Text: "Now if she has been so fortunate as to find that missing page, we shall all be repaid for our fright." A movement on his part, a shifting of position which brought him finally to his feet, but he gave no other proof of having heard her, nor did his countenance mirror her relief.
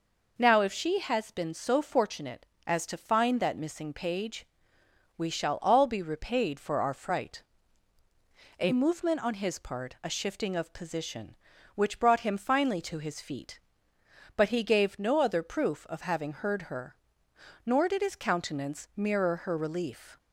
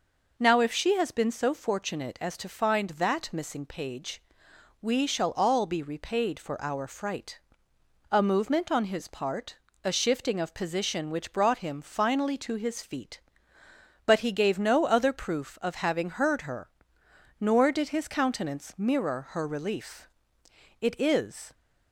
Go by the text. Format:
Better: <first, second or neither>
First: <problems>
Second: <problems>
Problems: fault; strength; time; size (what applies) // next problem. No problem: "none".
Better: first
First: none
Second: goes on to say "It is"; noticeable; from 20.8 s on; 0.72 s long